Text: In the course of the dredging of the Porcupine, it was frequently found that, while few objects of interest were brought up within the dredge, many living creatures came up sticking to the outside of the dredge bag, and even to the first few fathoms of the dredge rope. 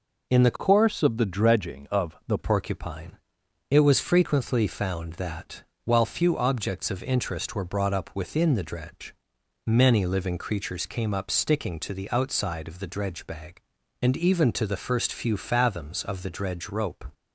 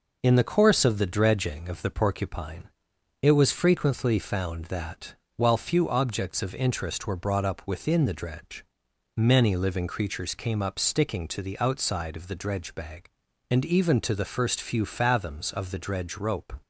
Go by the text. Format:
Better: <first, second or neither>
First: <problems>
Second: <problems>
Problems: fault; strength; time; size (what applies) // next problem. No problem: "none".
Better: second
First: changes voice from "course" to "the"; from 0.5 to 2.3 s; 1.8 s long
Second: none